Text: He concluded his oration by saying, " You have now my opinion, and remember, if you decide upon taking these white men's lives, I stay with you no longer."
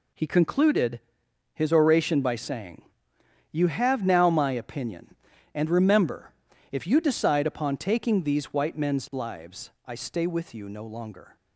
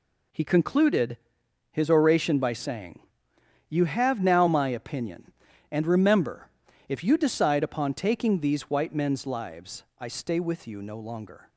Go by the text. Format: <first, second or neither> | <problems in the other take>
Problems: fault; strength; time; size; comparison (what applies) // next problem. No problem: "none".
neither | pauses between "concluded" and "his"; noticeable; the same in both